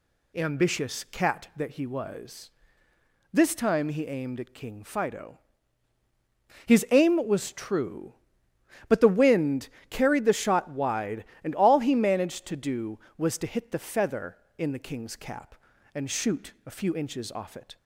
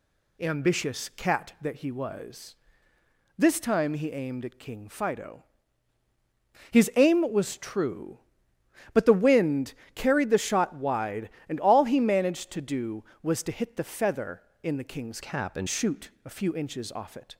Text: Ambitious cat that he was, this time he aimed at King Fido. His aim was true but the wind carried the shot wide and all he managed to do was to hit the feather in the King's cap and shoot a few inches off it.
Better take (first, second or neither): first